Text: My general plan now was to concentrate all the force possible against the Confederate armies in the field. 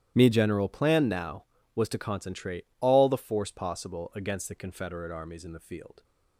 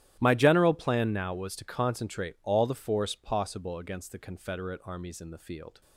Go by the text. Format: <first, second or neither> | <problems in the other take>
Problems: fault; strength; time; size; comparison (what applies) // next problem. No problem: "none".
second | starts louder than the rest; strong; until 1.1 s; 11.5 dB; strong in the second // says "Me" for "My"; at 0.1 s